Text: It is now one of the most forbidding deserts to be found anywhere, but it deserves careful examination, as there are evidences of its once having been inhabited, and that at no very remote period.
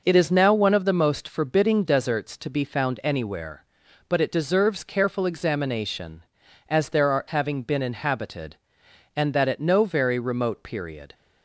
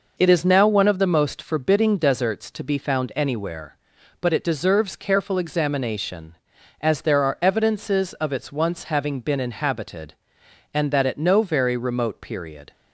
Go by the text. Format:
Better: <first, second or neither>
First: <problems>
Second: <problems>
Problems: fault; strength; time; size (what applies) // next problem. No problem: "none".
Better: second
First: skips "evidences of its once"; at 7.2 s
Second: none